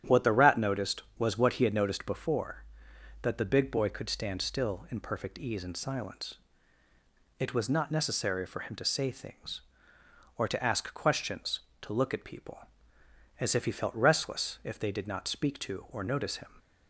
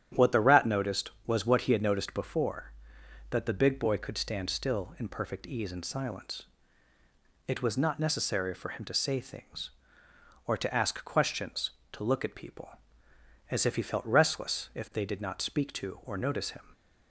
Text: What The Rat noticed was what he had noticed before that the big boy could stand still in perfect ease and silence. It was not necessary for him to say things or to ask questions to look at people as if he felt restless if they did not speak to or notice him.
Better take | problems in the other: neither | starts louder than the rest; strong; the same in both

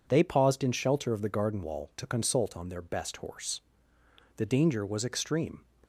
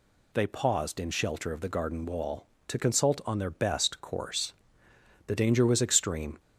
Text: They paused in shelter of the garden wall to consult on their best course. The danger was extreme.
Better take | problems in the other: second | says "horse" for "course"; at 3.1 s

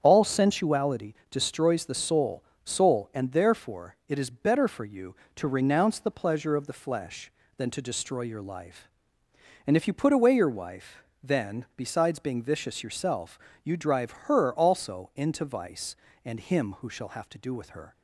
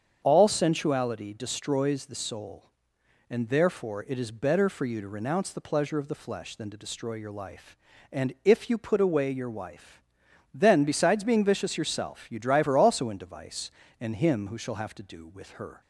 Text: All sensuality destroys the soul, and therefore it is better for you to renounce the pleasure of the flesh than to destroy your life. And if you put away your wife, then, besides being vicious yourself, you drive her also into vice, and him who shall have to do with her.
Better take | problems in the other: second | starts louder than the rest; strong; until 1.0 s; 8 dB; strong in the second // pauses between "sensuality" and "destroys"; slight; at 1.1 s; 0.16 s long // says "soul" twice; at 2.6 s

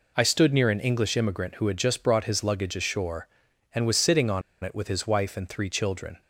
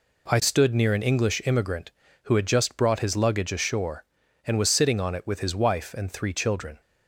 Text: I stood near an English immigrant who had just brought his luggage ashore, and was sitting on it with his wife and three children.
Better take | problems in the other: second | pauses between "on" and "it"; slight; at 4.4 s; 0.21 s long

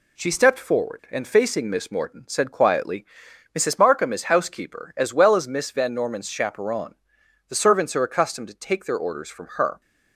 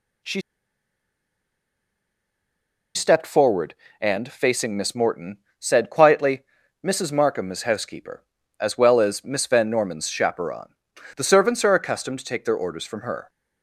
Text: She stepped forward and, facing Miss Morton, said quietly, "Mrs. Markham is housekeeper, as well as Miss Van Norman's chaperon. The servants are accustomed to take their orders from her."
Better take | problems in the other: first | pauses between "She" and "stepped"; strong; at 0.3 s; 2.5 s long

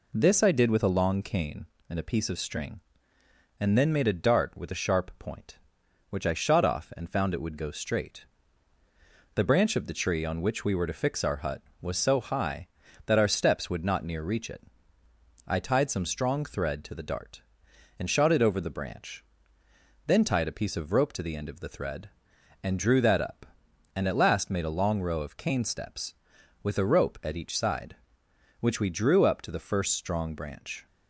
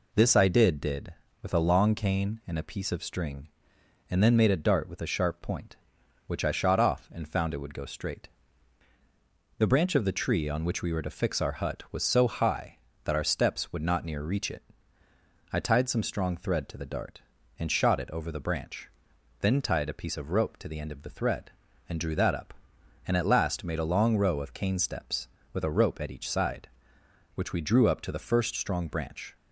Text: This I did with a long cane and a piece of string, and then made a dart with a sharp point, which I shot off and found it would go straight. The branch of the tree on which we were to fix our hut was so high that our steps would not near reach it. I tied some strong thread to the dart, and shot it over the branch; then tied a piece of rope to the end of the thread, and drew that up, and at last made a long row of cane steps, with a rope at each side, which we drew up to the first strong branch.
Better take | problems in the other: first | says "did" twice; at 0.8 s

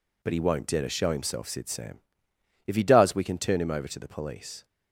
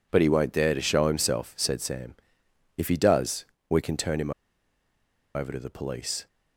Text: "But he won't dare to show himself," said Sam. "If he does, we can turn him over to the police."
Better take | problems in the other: first | pauses between "him" and "over"; at 4.3 s; 1.0 s long

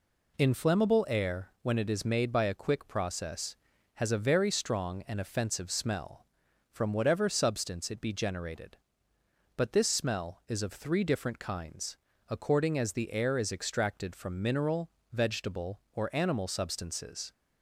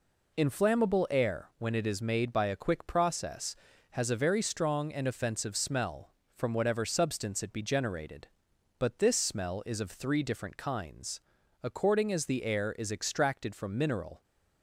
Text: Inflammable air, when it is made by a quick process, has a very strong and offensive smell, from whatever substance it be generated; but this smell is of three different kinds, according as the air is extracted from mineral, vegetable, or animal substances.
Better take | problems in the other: first | stops before "vegetable or animal substances"; at 14.2 s

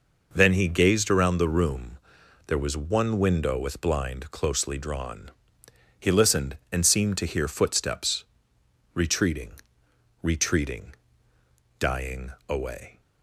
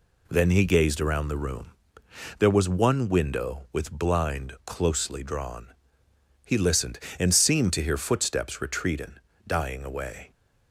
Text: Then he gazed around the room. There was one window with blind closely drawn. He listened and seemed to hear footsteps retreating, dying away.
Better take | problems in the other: second | pauses between "footsteps" and "retreating"; noticeable; at 8.2 s; 0.70 s long // says "retreating" twice; at 10.2 s // pauses between "dying" and "away"; slight; at 12.2 s; 0.18 s long

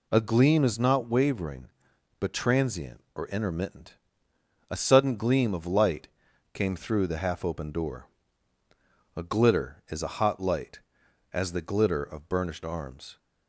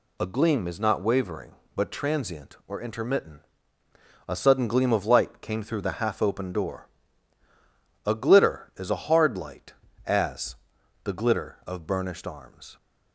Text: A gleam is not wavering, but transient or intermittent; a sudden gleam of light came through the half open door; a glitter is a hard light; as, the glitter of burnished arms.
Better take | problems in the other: second | pauses between "light" and "came"; noticeable; at 6.0 s; 0.46 s long // says "hot" for "hard"; at 10.1 s

